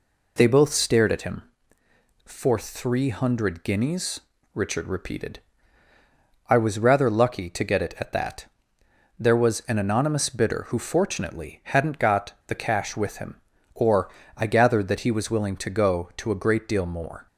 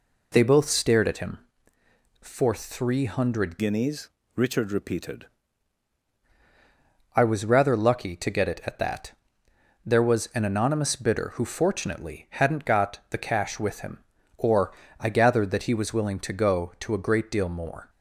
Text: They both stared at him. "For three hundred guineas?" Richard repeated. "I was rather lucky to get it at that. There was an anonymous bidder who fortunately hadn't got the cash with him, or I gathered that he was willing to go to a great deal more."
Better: first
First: pauses between "or" and "I"; slight; at 14.0 s; 0.26 s long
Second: changes voice from "guineas" to "repeated"; from 3.5 to 5.2 s; 1.7 s long // pauses between "or" and "I"; slight; at 14.7 s; 0.26 s long

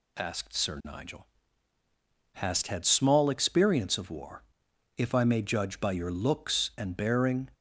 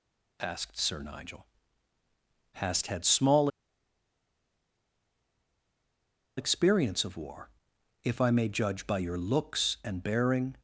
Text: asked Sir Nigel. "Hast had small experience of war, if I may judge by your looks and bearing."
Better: first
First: none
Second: pauses between "small" and "experience"; strong; at 3.4 s; 2.8 s long

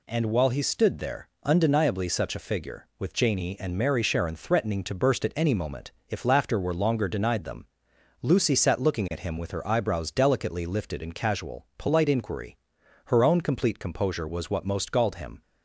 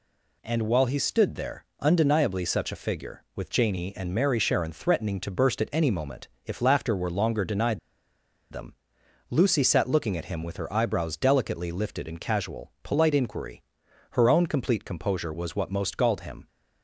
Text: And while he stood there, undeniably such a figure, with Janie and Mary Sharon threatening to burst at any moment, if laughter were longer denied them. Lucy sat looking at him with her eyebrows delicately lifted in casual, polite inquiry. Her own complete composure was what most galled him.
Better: first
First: none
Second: pauses between "denied" and "them"; noticeable; at 7.7 s; 0.73 s long

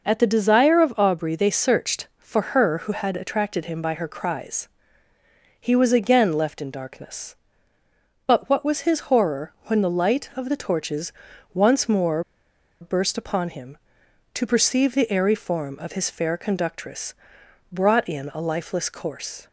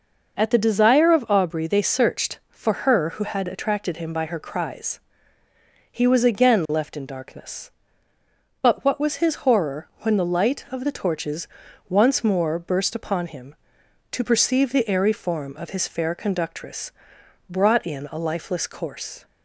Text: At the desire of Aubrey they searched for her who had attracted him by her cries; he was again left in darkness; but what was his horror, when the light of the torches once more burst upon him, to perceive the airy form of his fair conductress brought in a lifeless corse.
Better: second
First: pauses between "torches" and "once"; at 11.1 s; 0.40 s long // pauses between "more" and "burst"; noticeable; at 12.2 s; 0.59 s long // pauses between "conductress" and "brought"; noticeable; at 17.1 s; 0.56 s long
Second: pauses between "torches" and "once"; at 11.4 s; 0.40 s long // pauses between "conductress" and "brought"; noticeable; at 16.9 s; 0.56 s long

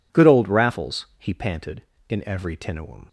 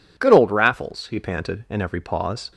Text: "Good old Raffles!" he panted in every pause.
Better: second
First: says "tinuum" for "pause"; at 2.5 s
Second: none

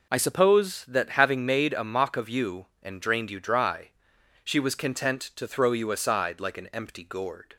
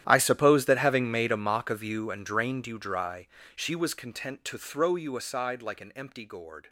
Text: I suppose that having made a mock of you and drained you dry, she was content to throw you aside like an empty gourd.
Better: first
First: none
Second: gets quieter; strong; throughout; 17.5 dB

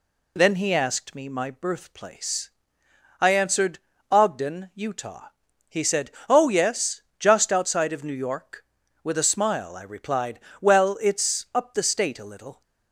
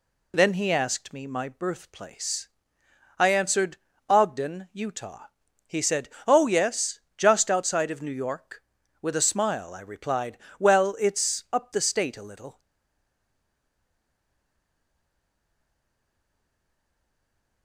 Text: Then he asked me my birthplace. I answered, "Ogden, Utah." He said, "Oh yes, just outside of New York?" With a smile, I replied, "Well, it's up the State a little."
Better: first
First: none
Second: stays silent after the last word; strong; from 12.5 s on; 5.1 s long

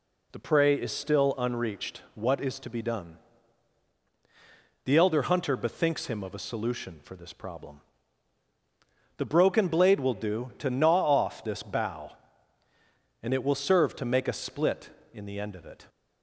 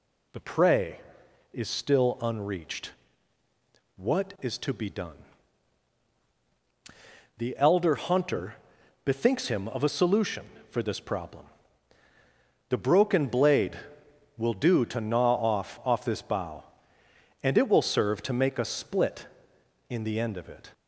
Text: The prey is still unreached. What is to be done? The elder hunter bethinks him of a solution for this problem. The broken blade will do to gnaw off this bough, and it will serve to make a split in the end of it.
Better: first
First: none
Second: pauses between "hunter" and "bethinks"; noticeable; at 8.5 s; 0.48 s long // says "off" twice; at 15.8 s

